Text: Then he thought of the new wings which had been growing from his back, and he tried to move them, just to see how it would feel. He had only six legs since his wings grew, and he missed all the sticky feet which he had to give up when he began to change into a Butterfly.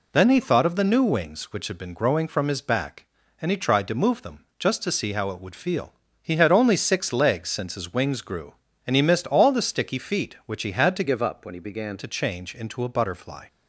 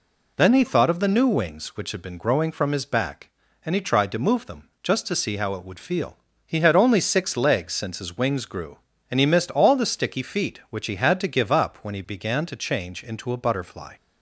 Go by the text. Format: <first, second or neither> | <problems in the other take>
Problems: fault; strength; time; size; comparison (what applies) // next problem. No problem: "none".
second | changes voice from "give" to "began"; from 11.0 to 11.9 s; 0.9 s long